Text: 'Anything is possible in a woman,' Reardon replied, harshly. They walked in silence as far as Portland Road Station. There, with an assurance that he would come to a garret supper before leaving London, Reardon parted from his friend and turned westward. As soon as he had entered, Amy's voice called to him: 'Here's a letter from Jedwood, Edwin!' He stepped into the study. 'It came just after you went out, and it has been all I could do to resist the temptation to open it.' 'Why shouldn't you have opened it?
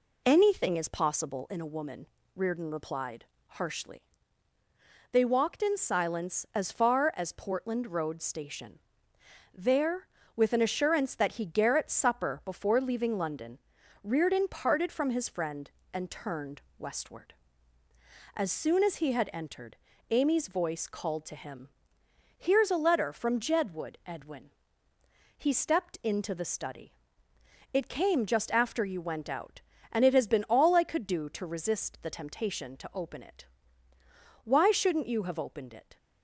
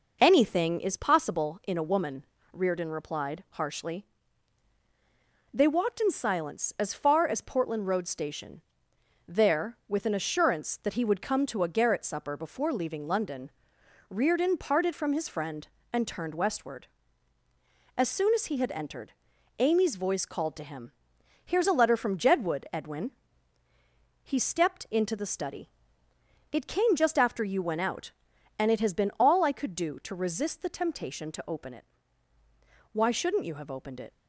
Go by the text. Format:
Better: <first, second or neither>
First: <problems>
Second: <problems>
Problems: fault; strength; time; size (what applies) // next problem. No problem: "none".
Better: second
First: skips "would come to a"; at 11.4 s // pauses between "turned" and "westward"; slight; at 16.6 s; 0.18 s long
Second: none